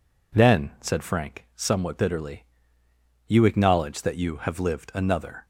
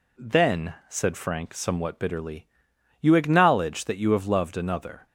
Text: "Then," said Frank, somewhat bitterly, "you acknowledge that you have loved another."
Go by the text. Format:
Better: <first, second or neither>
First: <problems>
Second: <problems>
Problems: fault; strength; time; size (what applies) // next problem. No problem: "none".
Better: second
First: says "lived" for "loved"; at 4.5 s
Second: none